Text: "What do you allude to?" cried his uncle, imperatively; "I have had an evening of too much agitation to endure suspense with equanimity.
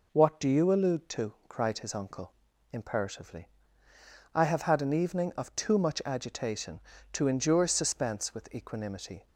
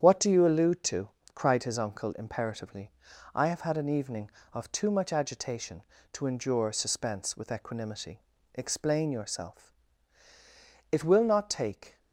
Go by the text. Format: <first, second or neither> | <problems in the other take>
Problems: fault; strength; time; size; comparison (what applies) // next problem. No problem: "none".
first | starts louder than the rest; strong; until 1.0 s; 8.5 dB // goes on to say "Explain yourself It will not take"; strong; from 8.5 s on; 3.4 s long